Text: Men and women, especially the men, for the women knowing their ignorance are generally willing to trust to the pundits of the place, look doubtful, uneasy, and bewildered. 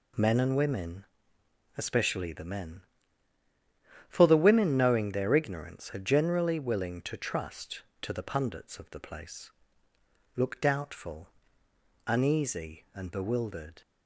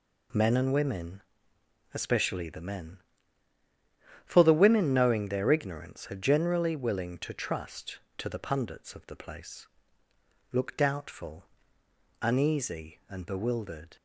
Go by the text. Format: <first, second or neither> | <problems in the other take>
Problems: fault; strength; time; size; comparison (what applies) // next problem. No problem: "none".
neither | none